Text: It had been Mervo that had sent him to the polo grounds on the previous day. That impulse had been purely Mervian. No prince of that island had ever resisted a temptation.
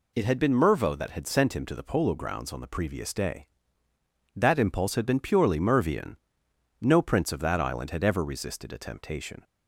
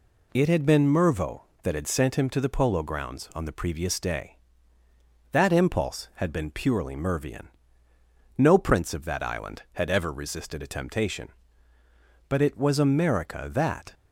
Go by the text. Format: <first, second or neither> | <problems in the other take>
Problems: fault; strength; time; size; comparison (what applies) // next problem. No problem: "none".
first | goes on to say "But it was America that"; from 12.2 s on; 1.6 s long